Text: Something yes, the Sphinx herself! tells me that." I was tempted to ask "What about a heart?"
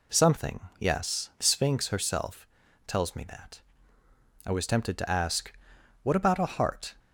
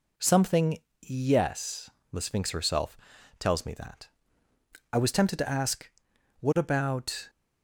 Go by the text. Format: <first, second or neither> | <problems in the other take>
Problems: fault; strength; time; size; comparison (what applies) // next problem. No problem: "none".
first | pauses between "Something" and "yes"; slight; at 0.7 s; 0.24 s long; slight in the first // pauses between "ask" and "What"; noticeable; at 5.8 s; 0.50 s long; noticeable in the first // stops before "a heart"; at 7.2 s